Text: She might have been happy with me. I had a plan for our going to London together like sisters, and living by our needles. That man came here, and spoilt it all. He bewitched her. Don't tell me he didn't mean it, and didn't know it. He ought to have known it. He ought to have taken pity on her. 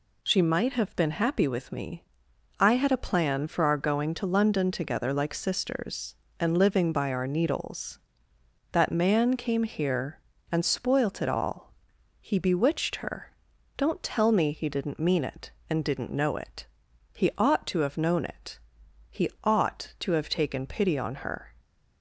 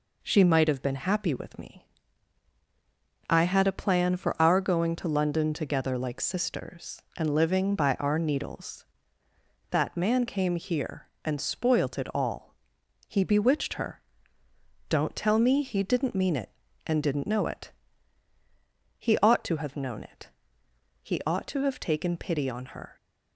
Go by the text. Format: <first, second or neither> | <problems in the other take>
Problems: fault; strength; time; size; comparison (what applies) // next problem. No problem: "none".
neither | none